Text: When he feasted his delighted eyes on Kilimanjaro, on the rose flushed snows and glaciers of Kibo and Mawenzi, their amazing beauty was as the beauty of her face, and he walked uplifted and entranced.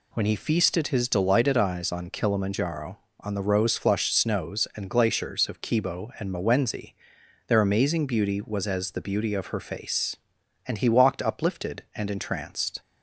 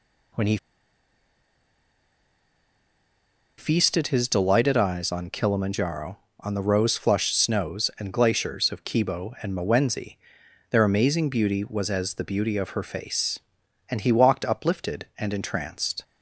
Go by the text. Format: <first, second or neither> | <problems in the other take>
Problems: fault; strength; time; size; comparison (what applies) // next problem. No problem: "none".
first | pauses between "he" and "feasted"; strong; at 0.5 s; 3.0 s long